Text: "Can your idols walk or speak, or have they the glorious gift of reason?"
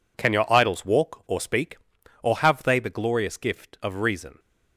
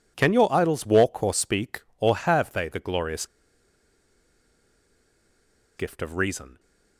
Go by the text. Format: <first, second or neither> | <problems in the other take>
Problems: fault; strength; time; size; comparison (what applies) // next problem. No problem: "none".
first | pauses between "glorious" and "gift"; strong; at 3.2 s; 2.5 s long